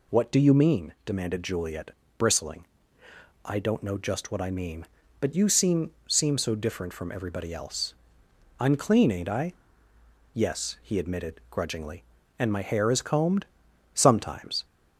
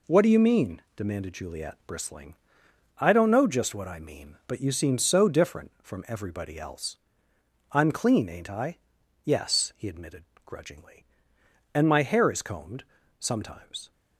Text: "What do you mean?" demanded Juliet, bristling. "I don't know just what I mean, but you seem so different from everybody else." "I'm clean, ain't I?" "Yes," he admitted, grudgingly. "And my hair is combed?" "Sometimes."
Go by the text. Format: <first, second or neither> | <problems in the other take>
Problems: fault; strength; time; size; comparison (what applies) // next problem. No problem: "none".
second | says "seem" twice; at 6.0 s